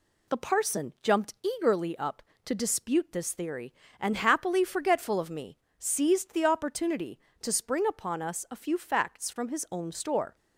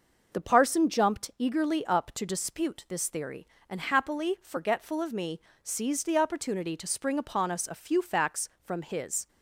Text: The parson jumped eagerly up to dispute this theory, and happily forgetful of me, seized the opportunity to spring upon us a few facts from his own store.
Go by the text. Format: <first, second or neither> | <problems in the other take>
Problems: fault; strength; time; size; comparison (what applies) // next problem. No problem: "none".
first | stops before "own store"; at 9.2 s